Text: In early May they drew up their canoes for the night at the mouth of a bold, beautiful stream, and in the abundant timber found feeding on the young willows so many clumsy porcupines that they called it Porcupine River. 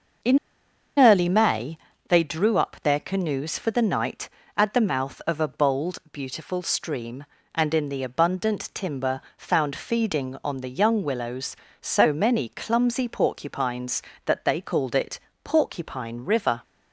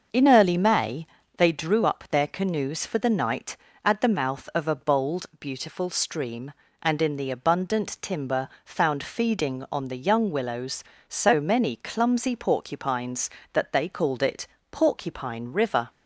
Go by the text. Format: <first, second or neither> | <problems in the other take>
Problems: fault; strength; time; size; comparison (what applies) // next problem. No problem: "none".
second | starts louder than the rest; until 2.1 s; 6.5 dB; also in the second // pauses between "In" and "early"; noticeable; at 0.3 s; 0.59 s long // pauses between "May" and "they"; slight; at 1.7 s; 0.32 s long; slight in the second // pauses between "timber" and "found"; slight; at 9.2 s; 0.16 s long; slight in the second // pauses between "it" and "Porcupine"; slight; at 15.1 s; 0.24 s long; slight in the second